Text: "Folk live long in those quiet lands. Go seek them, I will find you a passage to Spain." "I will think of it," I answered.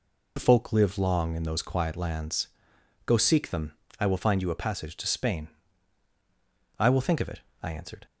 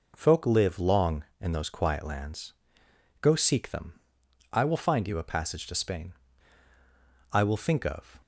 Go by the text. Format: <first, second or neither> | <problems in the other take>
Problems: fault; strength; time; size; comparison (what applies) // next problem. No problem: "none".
first | stops before "it I answered"; at 8.2 s